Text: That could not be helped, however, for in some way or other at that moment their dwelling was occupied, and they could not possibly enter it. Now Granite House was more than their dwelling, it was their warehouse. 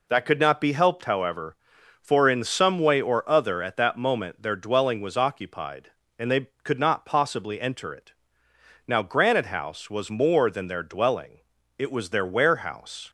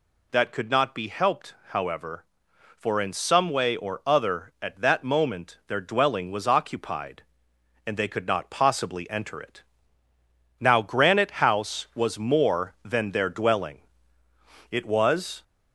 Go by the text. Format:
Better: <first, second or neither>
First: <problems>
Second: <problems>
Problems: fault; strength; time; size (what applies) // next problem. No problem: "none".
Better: first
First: none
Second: stops before "their warehouse"; at 15.4 s